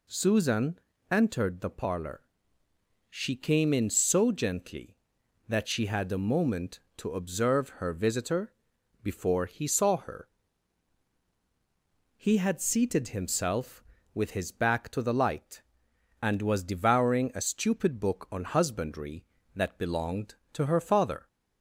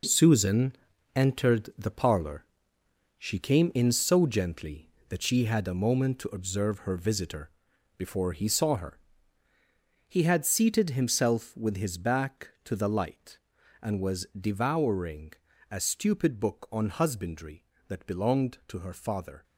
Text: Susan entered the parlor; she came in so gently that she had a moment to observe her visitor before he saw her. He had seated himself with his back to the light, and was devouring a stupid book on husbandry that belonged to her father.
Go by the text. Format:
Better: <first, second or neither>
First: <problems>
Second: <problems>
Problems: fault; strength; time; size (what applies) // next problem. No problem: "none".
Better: first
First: pauses between "Susan" and "entered"; slight; at 0.7 s; 0.32 s long // pauses between "visitor" and "before"; noticeable; at 8.5 s; 0.48 s long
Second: gets quieter; strong; throughout; 9 dB // pauses between "Susan" and "entered"; at 0.7 s; 0.40 s long // pauses between "visitor" and "before"; noticeable; at 7.4 s; 0.48 s long // pauses between "devouring" and "a"; slight; at 15.3 s; 0.36 s long